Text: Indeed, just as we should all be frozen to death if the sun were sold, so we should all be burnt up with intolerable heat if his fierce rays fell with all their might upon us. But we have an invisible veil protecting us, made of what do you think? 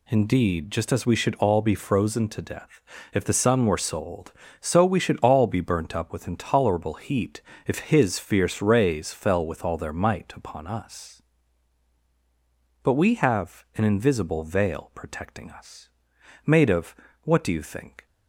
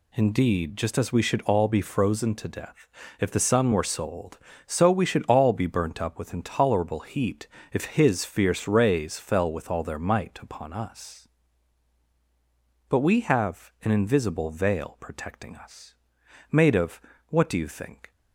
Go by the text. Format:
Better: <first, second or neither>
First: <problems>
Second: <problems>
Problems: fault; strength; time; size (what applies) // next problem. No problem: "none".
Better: neither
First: pauses between "death" and "if"; slight; at 2.8 s; 0.32 s long // pauses between "heat" and "if"; slight; at 7.4 s; 0.26 s long // pauses between "of" and "what"; slight; at 16.9 s; 0.26 s long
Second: pauses between "death" and "if"; slight; at 2.8 s; 0.32 s long // pauses between "heat" and "if"; slight; at 7.4 s; 0.26 s long // pauses between "of" and "what"; slight; at 17.0 s; 0.26 s long